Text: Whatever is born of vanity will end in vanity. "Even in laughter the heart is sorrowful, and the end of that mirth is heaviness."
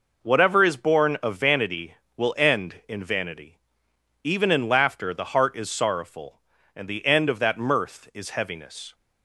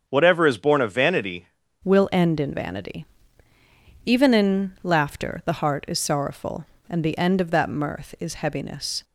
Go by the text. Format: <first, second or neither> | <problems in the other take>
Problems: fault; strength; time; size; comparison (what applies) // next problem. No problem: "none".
first | starts louder than the rest; strong; until 1.0 s; 7 dB // changes voice at "will"; from 1.8 s on; 7.2 s long